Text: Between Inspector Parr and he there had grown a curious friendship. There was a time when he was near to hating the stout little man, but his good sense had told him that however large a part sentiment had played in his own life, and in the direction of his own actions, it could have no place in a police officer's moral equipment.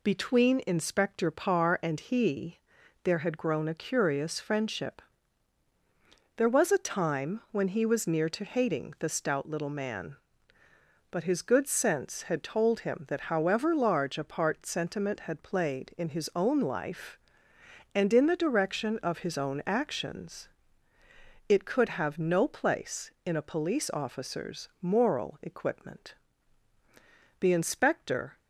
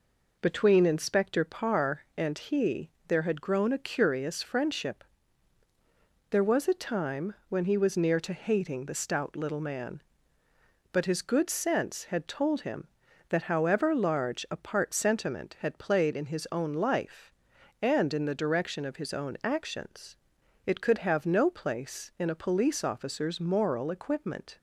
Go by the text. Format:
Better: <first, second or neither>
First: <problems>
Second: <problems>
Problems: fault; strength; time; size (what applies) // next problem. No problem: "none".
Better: second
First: pauses between "he" and "there"; at 2.5 s; 0.44 s long // goes on to say "The inspector"; noticeable; from 27.3 s on; 0.98 s long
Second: pauses between "he" and "there"; slight; at 2.8 s; 0.18 s long